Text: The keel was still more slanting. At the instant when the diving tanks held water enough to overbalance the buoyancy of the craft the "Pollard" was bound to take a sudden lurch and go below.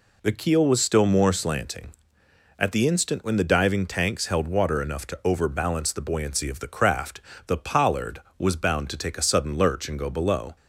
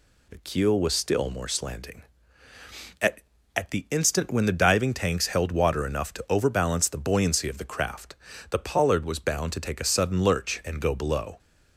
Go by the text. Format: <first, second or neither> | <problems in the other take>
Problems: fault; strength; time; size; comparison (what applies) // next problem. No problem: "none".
first | says "At" twice; at 3.5 s // pauses between "craft" and "the"; slight; at 8.1 s; 0.36 s long; slight in the first